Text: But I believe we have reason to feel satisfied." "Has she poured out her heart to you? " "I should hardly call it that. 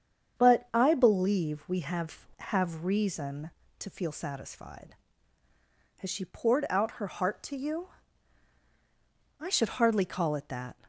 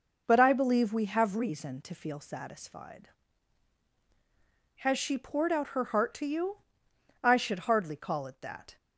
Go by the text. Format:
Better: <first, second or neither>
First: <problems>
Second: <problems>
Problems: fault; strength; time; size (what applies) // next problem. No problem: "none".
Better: second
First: starts louder than the rest; strong; until 1.4 s; 8 dB // says "have" twice; at 2.3 s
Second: none